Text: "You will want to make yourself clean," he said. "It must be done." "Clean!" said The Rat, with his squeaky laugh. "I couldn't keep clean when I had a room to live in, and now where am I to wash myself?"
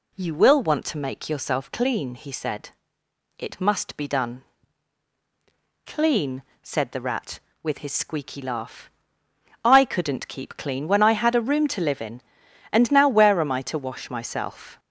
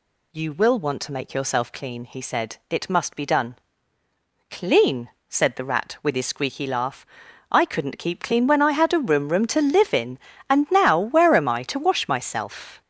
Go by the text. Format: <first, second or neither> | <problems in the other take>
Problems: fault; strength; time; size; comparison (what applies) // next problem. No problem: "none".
first | says "room" twice; at 9.2 s